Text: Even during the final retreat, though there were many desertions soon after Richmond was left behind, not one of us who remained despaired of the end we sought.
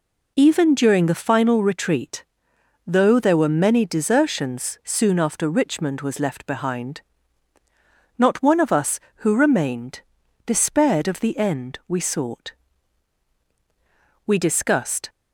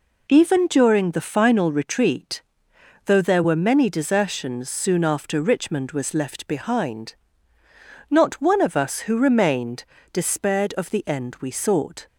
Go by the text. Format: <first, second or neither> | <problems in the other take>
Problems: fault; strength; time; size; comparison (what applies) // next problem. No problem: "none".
second | pauses between "remained" and "despaired"; at 10.0 s; 0.44 s long; slight in the second // goes on to say "We discussed"; noticeable; from 14.2 s on; 0.82 s long